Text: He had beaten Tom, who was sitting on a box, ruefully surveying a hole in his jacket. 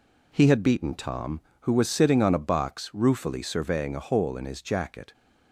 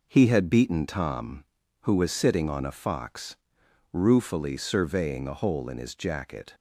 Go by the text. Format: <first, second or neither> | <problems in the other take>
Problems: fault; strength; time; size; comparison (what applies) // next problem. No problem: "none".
first | says "fox" for "box"; at 2.7 s